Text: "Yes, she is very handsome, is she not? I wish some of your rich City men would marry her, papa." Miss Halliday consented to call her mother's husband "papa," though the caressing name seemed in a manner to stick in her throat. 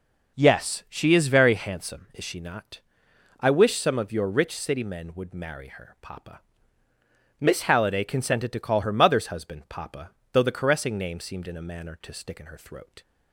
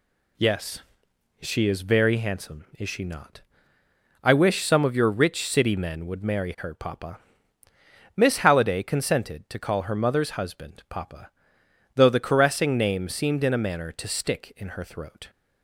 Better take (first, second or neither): neither